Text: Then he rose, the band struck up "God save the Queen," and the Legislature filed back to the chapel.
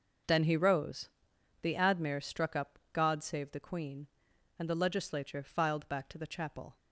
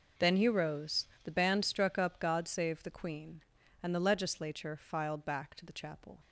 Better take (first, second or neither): second